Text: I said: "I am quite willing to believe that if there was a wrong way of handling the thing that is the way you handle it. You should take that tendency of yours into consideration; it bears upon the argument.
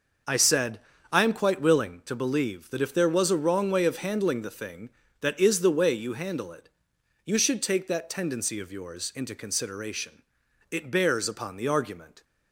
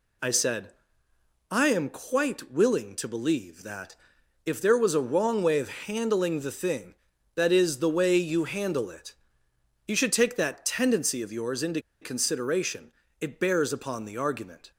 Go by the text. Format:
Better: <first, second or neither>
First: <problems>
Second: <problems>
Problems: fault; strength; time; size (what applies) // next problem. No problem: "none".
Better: first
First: none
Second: pauses between "that" and "if"; noticeable; at 3.9 s; 0.50 s long // pauses between "into" and "consideration"; slight; at 11.7 s; 0.22 s long